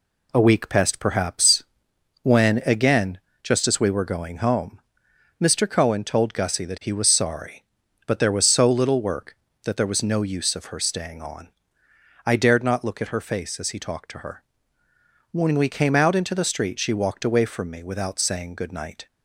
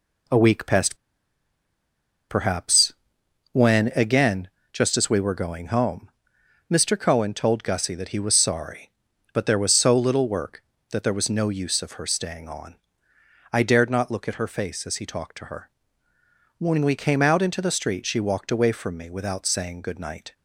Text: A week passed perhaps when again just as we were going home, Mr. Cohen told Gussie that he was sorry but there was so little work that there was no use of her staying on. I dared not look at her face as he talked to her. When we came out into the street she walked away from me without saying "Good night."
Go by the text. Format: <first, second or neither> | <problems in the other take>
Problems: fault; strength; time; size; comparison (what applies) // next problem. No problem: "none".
first | pauses between "passed" and "perhaps"; strong; at 0.9 s; 1.3 s long // pauses between "perhaps" and "when"; noticeable; at 2.9 s; 0.58 s long; noticeable in the first // pauses between "again" and "just"; slight; at 4.4 s; 0.22 s long; slight in the first